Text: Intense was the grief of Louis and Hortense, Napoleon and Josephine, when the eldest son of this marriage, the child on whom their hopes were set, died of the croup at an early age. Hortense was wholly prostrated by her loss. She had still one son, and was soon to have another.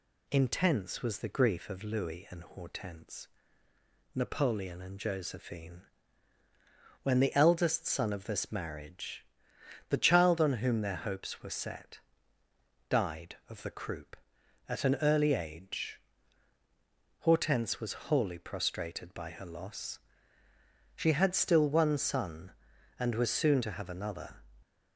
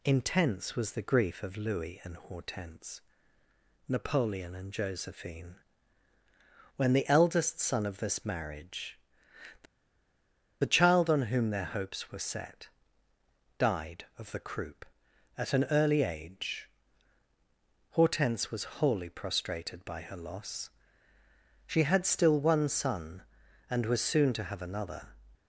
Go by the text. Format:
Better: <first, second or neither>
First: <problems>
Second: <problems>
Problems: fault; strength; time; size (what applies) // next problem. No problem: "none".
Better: first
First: none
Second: pauses between "the" and "child"; at 9.6 s; 0.98 s long